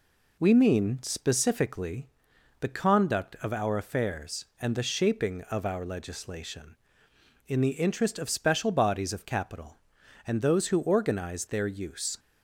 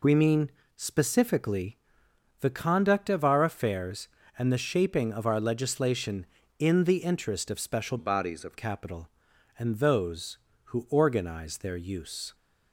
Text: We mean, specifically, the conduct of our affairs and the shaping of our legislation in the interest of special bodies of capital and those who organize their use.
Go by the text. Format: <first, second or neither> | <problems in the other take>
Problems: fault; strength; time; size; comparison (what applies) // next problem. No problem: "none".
first | changes voice from "bodies" to "of"; from 7.9 to 8.5 s; 0.6 s long